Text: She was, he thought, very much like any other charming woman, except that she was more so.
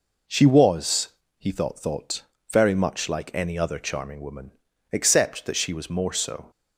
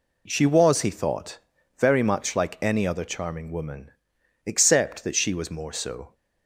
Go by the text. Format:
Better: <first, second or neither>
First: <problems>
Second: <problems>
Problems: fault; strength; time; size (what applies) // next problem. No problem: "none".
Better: second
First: says "thought" twice; at 1.7 s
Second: none